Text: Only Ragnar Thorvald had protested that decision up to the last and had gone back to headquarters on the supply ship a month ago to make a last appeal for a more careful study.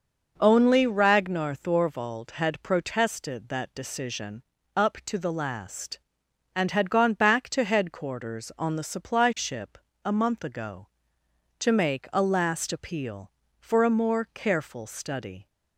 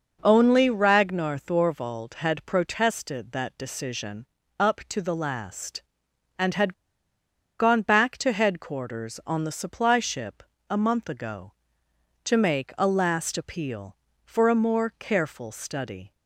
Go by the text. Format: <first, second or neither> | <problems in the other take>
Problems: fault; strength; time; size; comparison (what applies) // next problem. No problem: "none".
first | pauses between "decision" and "up"; slight; at 4.2 s; 0.32 s long; slight in the first // pauses between "had" and "gone"; noticeable; at 6.7 s; 0.85 s long // pauses between "ship" and "a"; slight; at 10.4 s; 0.28 s long; slight in the first